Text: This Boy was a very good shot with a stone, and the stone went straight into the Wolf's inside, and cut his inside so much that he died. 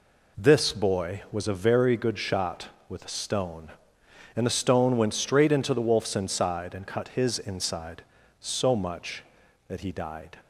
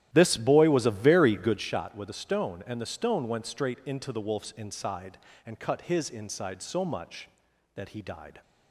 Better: first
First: none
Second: starts louder than the rest; strong; until 1.8 s; 12.5 dB

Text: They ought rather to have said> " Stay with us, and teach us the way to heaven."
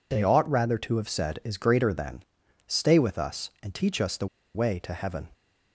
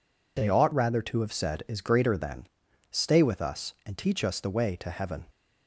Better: second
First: pauses between "the" and "way"; slight; at 4.2 s; 0.28 s long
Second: none

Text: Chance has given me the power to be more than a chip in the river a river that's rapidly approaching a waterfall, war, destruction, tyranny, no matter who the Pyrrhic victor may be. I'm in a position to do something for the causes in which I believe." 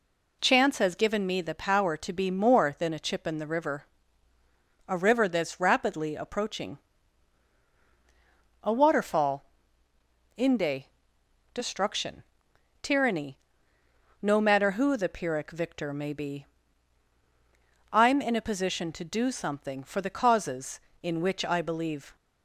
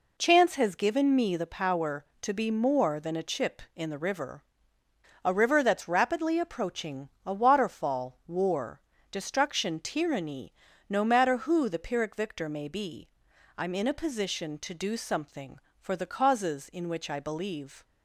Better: second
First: pauses between "river" and "a"; at 3.8 s; 1.0 s long // pauses between "approaching" and "a"; strong; at 6.7 s; 1.8 s long // says "inde" for "war"; at 10.3 s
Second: pauses between "river" and "a"; noticeable; at 4.4 s; 0.82 s long // pauses between "approaching" and "a"; slight; at 7.0 s; 0.16 s long

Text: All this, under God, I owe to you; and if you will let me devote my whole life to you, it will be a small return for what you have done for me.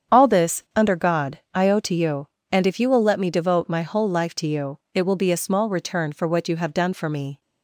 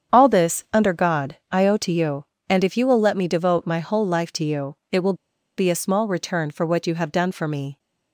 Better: first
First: starts louder than the rest; strong; until 1.2 s; 8 dB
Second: starts louder than the rest; strong; until 1.2 s; 8 dB // pauses between "will" and "be"; at 5.1 s; 0.44 s long

